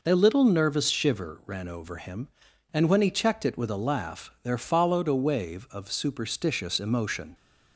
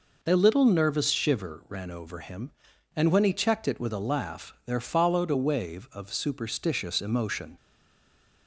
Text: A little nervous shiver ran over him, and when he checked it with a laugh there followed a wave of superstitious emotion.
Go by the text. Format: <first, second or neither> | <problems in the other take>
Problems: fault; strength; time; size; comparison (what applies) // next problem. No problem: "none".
first | stays silent after the last word; slight; from 7.5 s on; 0.9 s long